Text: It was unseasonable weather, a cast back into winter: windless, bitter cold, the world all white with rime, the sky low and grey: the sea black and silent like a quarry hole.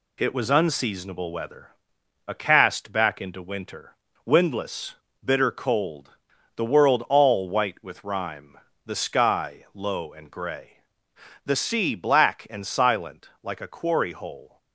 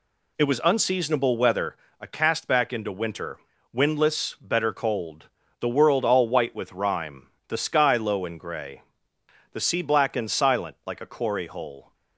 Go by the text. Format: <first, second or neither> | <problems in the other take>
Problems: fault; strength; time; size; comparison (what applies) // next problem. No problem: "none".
first | says "better" for "bitter"; at 4.4 s